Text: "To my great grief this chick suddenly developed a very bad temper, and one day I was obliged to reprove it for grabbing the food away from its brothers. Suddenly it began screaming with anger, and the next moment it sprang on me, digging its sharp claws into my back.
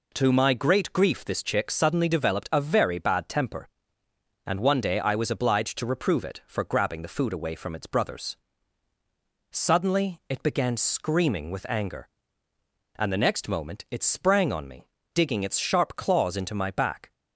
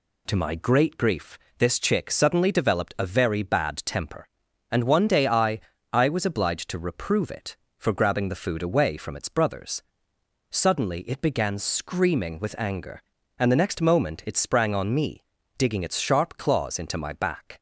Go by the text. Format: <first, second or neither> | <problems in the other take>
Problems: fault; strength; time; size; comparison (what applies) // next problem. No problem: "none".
first | pauses between "grief" and "this"; slight; at 1.3 s; 0.22 s long // says "I" twice; at 5.9 s